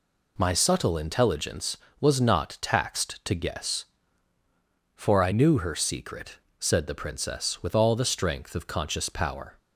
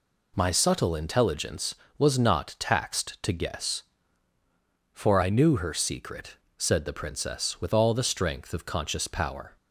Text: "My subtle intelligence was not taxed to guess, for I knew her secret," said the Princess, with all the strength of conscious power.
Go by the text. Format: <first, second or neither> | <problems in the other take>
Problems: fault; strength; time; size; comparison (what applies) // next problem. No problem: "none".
neither | none